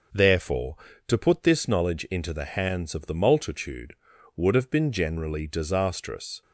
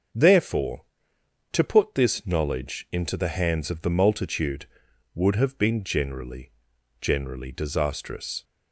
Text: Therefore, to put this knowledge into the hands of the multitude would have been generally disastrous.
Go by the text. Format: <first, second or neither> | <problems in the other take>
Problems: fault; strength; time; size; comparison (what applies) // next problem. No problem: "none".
first | starts louder than the rest; until 1.8 s; 7 dB // says "generally" twice; at 6.9 s